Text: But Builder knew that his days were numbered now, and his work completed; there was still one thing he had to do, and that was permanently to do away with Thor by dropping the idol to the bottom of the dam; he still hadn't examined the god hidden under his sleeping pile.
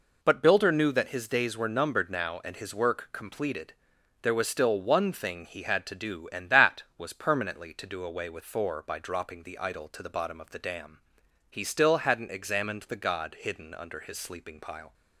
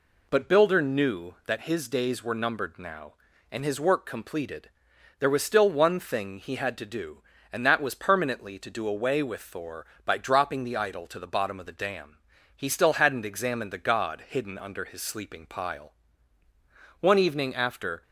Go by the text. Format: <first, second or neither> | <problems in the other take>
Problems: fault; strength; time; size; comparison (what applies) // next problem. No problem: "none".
first | goes on to say "One evening after"; noticeable; from 16.9 s on; 1.0 s long